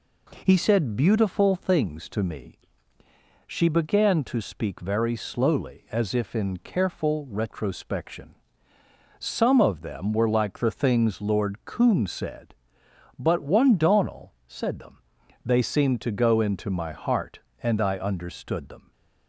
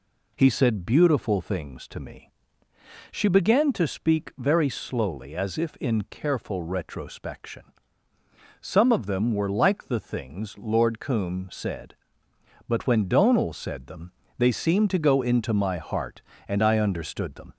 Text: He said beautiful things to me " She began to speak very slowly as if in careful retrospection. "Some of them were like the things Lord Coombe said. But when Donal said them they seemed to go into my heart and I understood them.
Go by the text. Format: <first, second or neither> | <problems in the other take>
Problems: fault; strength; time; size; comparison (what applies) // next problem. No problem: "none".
second | says "one" for "when"; at 13.4 s // pauses between "them" and "they"; noticeable; at 14.9 s; 0.46 s long; slight in the second